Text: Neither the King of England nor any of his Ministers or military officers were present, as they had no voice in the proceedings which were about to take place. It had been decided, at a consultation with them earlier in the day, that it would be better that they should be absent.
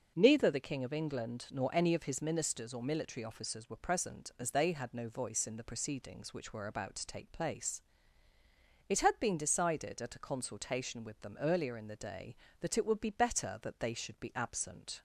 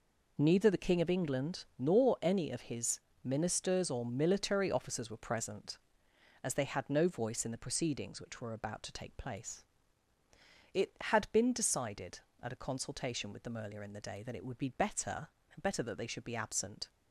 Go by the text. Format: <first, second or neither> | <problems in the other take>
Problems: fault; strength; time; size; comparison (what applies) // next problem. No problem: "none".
first | pauses between "his" and "Ministers"; slight; at 2.9 s; 0.24 s long // says "better" twice; at 15.5 s